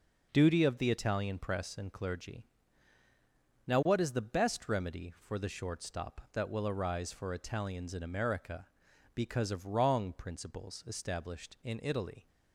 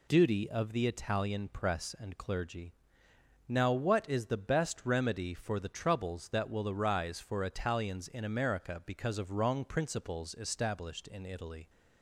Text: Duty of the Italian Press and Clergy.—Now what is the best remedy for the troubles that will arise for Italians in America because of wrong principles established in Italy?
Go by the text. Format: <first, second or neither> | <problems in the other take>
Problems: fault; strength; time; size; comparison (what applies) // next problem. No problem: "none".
second | says "shortstop" for "troubles"; at 5.4 s